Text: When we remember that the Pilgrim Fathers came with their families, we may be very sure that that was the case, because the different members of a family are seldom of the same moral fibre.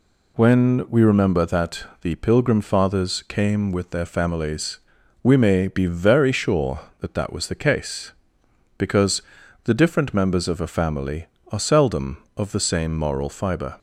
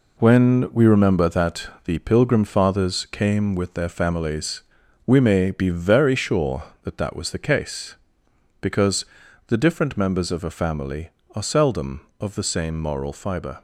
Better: first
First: pauses between "that" and "the"; slight; at 1.8 s; 0.16 s long // pauses between "because" and "the"; at 9.2 s; 0.40 s long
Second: gets quieter; throughout; 6.5 dB // pauses between "that" and "the"; slight; at 1.6 s; 0.16 s long // pauses between "because" and "the"; at 9.0 s; 0.40 s long

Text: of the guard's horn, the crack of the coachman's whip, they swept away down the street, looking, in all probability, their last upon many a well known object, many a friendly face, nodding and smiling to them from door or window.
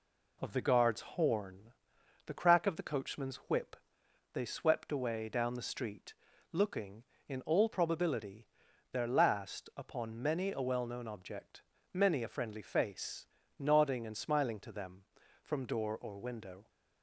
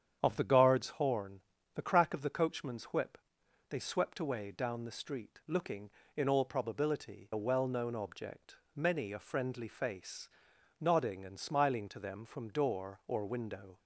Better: first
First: none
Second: starts louder than the rest; strong; until 1.2 s; 8.5 dB // skips "their last upon many"; at 7.3 s

